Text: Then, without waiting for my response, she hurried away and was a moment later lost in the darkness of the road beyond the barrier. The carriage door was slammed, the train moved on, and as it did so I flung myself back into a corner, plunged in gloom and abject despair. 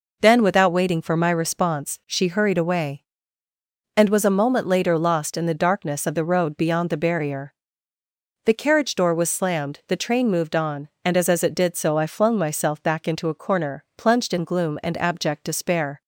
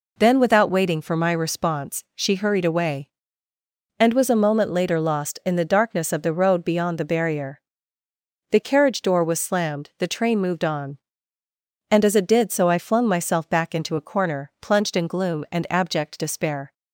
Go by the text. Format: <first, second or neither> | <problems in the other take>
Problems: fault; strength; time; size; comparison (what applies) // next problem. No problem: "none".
second | says "as" twice; at 11.2 s